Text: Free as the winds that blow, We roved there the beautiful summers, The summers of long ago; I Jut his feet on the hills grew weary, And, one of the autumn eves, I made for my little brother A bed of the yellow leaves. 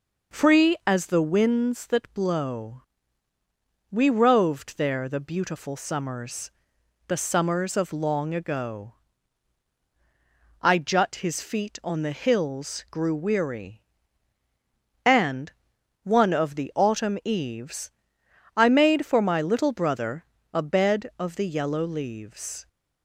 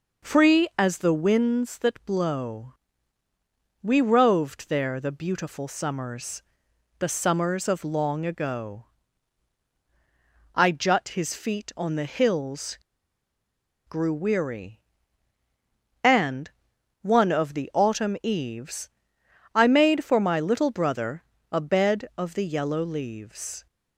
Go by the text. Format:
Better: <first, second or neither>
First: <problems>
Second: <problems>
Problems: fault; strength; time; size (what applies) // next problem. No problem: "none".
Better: first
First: pauses between "brother" and "A"; slight; at 20.2 s; 0.28 s long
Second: pauses between "hills" and "grew"; at 12.7 s; 1.1 s long // pauses between "brother" and "A"; slight; at 21.2 s; 0.28 s long